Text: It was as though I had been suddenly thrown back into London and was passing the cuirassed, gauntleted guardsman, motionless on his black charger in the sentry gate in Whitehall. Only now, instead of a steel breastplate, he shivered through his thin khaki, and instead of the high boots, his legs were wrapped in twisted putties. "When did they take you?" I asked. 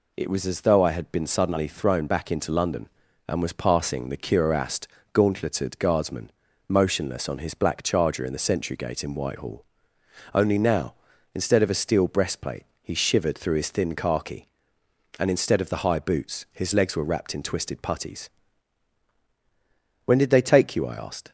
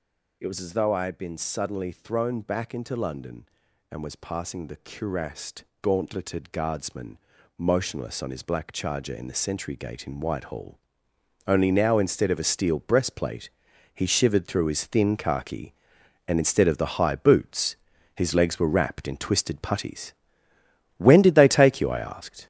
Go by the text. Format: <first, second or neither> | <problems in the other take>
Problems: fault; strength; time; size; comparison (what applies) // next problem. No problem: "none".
first | gets louder; throughout; 7 dB